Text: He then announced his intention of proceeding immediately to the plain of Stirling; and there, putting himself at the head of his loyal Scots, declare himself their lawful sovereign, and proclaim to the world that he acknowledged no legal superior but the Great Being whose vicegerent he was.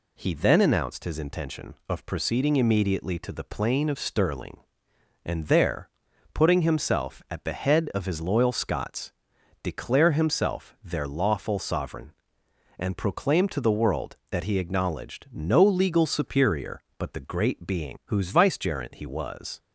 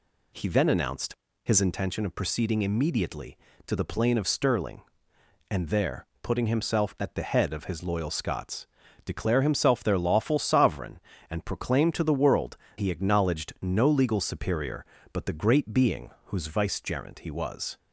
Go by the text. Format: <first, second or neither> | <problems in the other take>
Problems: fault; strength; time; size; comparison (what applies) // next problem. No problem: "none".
first | pauses between "announced" and "his"; slight; at 1.1 s; 0.30 s long // skips "that"; at 12.6 s // pauses between "Being" and "whose"; slight; at 16.0 s; 0.16 s long